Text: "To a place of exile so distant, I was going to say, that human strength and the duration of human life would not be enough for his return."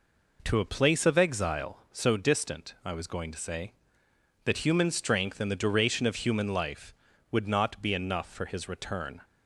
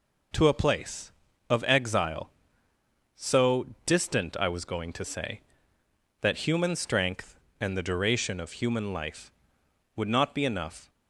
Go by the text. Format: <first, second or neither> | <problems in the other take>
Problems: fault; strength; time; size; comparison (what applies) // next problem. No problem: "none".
first | pauses between "so" and "distant"; slight; at 3.6 s; 0.20 s long // stops before "for his return"; at 10.8 s